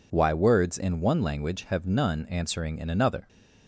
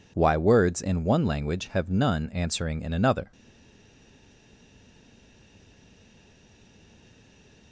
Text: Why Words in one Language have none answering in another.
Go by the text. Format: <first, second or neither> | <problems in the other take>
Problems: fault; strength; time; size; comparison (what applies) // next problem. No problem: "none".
first | stays silent after the last word; strong; from 3.3 s on; 4.4 s long